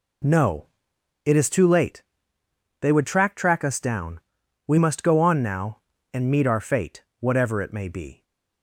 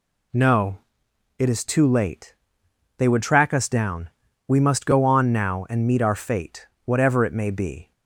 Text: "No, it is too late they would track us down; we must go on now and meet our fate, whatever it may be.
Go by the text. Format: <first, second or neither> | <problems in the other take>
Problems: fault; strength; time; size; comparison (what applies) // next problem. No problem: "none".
second | pauses between "late" and "they"; noticeable; at 2.0 s; 0.76 s long; noticeable in the second // says "track" twice; at 3.3 s